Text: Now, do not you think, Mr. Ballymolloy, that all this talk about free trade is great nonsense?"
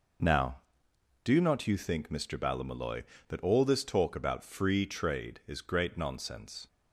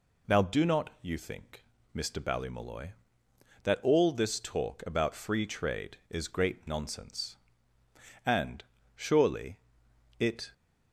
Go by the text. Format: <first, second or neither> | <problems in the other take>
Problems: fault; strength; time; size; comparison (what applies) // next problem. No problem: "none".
first | goes on to say "And surely it"; strong; from 8.2 s on; 2.2 s long